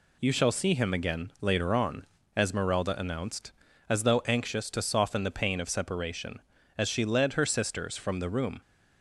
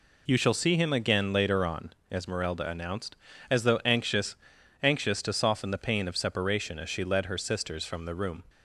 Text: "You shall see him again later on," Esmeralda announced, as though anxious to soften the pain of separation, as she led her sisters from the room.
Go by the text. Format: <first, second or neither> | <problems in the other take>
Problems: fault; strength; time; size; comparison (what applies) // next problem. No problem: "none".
first | says "anxious" twice; at 4.8 s